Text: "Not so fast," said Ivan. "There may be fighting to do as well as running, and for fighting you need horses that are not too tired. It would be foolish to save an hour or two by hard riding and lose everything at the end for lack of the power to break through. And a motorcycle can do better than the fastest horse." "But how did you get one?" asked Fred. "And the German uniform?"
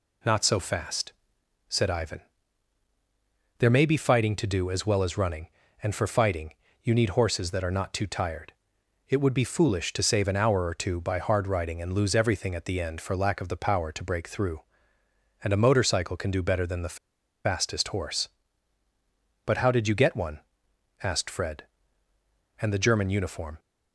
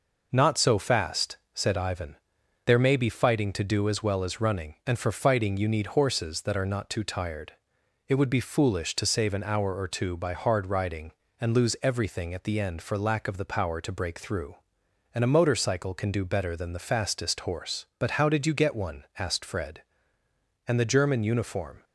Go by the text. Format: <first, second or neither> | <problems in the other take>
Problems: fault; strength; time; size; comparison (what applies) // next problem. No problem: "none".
second | pauses between "fighting" and "you"; slight; at 6.5 s; 0.30 s long // pauses between "the" and "fastest"; noticeable; at 16.9 s; 0.48 s long